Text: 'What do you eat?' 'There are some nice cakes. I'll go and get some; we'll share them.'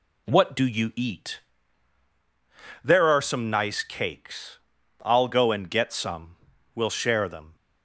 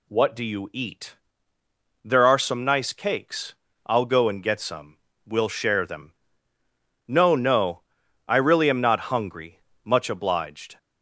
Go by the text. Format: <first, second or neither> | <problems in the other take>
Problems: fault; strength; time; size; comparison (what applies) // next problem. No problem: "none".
first | goes on to say "No no I really am not hungry much obliged"; strong; from 7.0 s on; 3.7 s long